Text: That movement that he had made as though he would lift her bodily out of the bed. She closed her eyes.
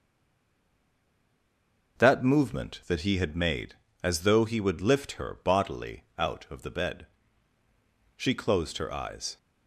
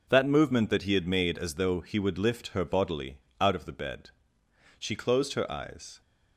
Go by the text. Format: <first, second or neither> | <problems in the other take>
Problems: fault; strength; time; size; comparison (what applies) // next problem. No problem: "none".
second | stays silent before the first word; noticeable; until 1.9 s; 1.9 s long // pauses between "bodily" and "out"; slight; at 6.0 s; 0.16 s long; slight in the second